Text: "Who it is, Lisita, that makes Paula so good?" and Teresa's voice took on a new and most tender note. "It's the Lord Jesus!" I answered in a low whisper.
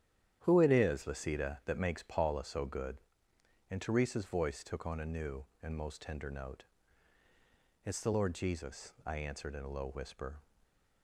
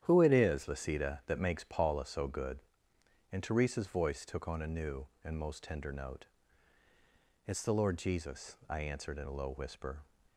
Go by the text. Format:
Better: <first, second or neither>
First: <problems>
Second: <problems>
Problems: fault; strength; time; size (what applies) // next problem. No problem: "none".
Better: neither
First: starts louder than the rest; strong; until 1.4 s; 10 dB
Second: starts louder than the rest; strong; until 1.0 s; 10 dB